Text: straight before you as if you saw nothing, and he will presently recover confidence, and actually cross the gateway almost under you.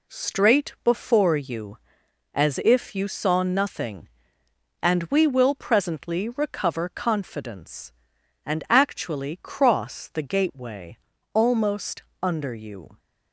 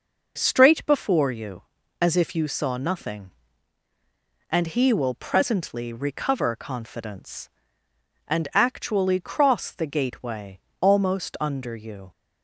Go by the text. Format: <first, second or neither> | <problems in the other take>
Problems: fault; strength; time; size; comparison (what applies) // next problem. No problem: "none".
second | says "we" for "he"; at 5.0 s // pauses between "gateway" and "almost"; at 10.9 s; 0.38 s long; slight in the second // pauses between "almost" and "under"; slight; at 12.0 s; 0.20 s long